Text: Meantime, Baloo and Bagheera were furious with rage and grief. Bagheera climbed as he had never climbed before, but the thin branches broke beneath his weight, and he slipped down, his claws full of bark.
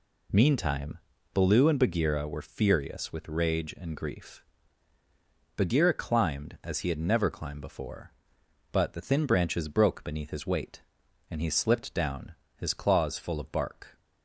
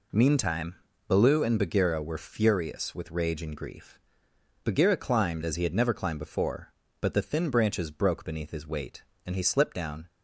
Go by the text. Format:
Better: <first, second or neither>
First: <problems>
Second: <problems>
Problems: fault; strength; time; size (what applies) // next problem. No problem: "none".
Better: first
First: none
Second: stops before "his claws full of bark"; at 10.0 s